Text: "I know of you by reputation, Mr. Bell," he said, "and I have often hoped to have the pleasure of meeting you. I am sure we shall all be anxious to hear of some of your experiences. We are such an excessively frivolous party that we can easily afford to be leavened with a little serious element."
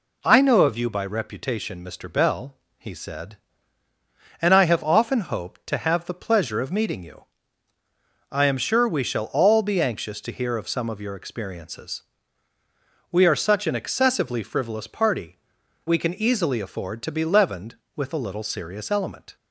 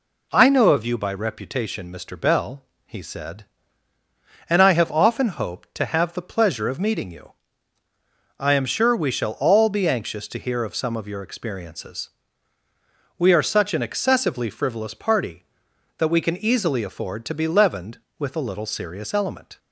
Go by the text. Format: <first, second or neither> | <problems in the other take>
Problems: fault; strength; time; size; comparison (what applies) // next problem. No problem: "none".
second | skips "that"; at 15.6 s